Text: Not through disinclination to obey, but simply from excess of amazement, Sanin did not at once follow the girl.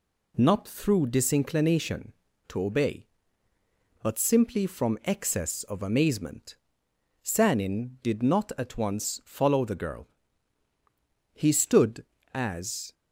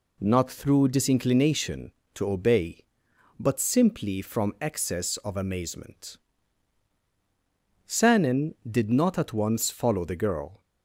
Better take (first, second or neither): second